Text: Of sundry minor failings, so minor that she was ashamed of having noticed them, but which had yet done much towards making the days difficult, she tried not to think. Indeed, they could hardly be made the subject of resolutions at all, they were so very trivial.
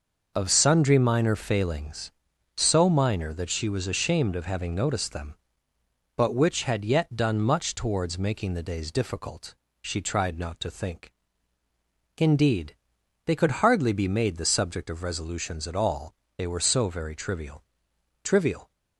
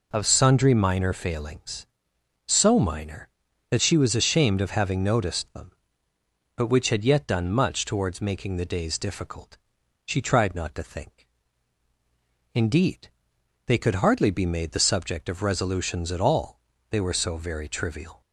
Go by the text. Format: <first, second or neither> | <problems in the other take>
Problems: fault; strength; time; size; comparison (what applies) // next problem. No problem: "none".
second | says "trivial" twice; at 18.2 s